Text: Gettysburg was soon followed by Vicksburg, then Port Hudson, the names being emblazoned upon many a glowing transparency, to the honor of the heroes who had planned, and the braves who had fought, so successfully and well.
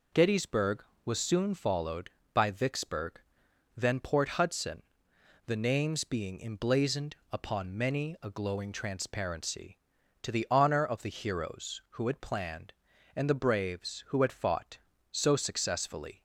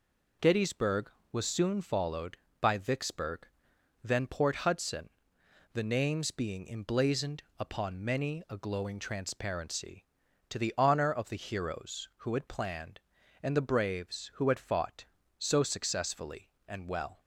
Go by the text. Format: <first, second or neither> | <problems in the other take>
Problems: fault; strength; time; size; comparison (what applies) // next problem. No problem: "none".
second | pauses between "emblazoned" and "upon"; slight; at 7.1 s; 0.16 s long; slight in the second // stops before "and well"; at 16.1 s